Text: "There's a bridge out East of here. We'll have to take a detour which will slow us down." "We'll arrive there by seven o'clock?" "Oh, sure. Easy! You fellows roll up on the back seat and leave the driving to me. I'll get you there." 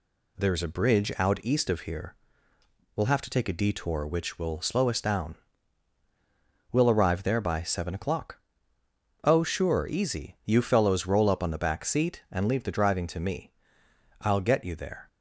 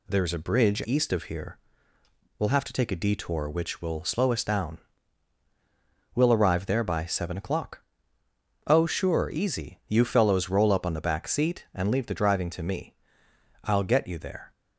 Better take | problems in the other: first | skips "out"; at 0.8 s

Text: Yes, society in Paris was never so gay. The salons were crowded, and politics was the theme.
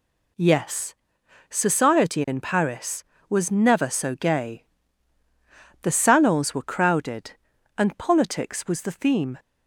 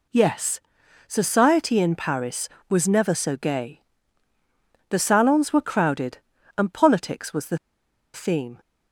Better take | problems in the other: first | pauses between "the" and "theme"; noticeable; at 7.5 s; 0.56 s long

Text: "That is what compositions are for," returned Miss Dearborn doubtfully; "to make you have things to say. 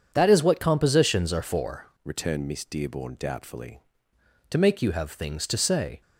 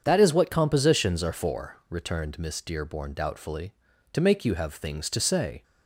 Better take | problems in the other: second | starts louder than the rest; strong; until 1.1 s; 7.5 dB; also in the second // changes voice from "returned" to "doubtfully"; from 2.0 to 3.7 s; 1.7 s long

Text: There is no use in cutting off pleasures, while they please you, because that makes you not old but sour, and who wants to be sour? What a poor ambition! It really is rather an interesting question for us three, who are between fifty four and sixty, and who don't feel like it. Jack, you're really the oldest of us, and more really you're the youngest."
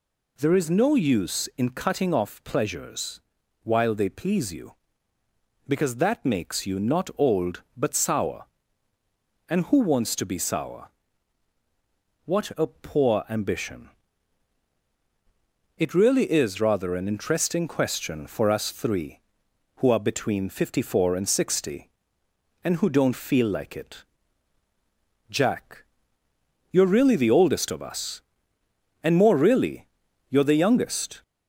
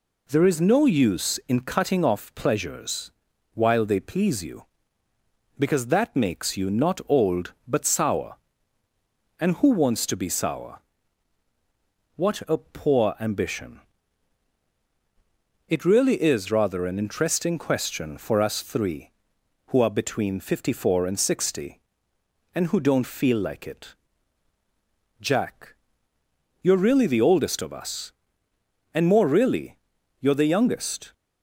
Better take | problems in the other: second | gets louder; slight; throughout; 2 dB // pauses between "really" and "you're"; at 29.8 s; 0.42 s long; also in the second

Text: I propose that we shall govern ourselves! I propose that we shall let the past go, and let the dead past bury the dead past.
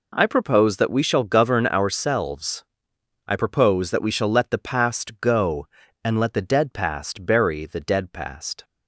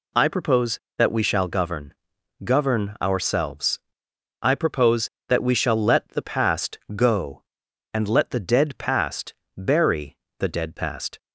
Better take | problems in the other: first | says "govern" twice; at 2.4 s // pauses between "past" and "go"; slight; at 6.7 s; 0.16 s long // pauses between "past" and "bury"; slight; at 9.3 s; 0.24 s long // pauses between "bury" and "the"; slight; at 10.1 s; 0.22 s long

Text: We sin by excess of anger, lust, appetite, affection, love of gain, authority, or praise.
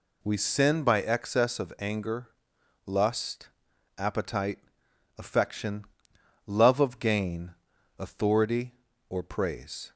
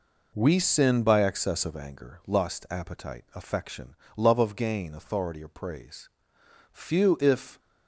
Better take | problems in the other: first | goes on to say "Few if"; noticeable; from 6.7 s on; 0.88 s long

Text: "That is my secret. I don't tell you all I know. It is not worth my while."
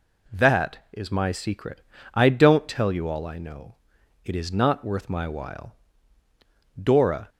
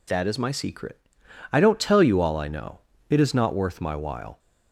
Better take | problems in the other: second | goes on to say "Dora"; from 6.7 s on; 0.52 s long

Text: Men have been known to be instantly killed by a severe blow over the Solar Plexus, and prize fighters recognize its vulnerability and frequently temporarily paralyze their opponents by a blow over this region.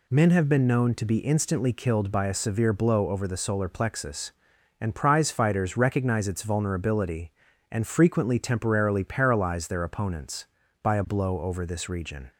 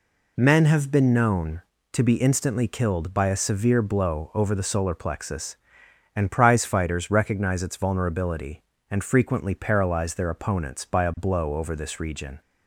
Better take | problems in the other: first | skips "temporarily"; at 9.5 s

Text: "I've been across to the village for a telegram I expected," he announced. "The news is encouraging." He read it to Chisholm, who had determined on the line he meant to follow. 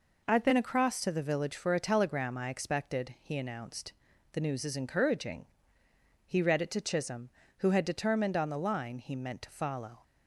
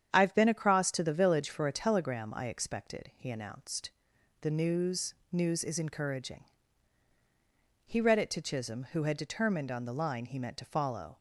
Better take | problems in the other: first | starts louder than the rest; strong; until 1.1 s; 8.5 dB // says "news" twice; at 5.3 s

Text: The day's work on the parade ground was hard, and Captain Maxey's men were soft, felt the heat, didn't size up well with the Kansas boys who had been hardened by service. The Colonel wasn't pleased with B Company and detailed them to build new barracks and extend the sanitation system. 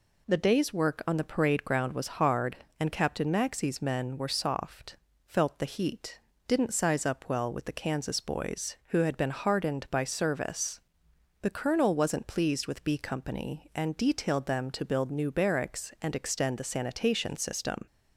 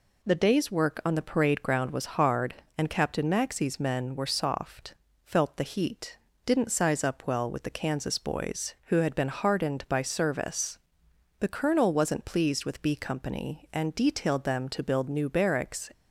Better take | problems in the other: first | stops before "and extend the sanitation system"; at 15.9 s

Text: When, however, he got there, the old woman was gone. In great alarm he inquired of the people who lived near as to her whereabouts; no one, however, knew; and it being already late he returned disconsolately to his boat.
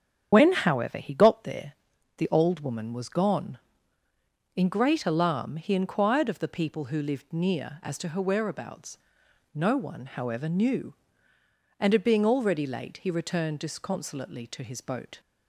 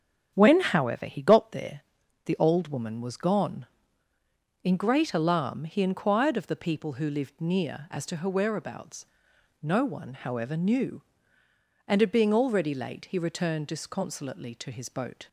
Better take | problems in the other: second | loses the start of "When"; at 0.3 s; 65 ms // starts louder than the rest; strong; until 1.3 s; 8.5 dB; strong in the second

